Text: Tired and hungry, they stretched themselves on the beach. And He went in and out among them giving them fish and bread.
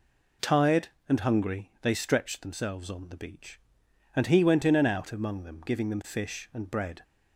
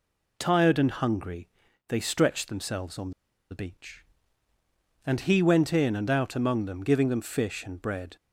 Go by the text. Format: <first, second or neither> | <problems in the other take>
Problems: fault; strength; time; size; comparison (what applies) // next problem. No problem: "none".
first | pauses between "on" and "the"; at 3.1 s; 0.40 s long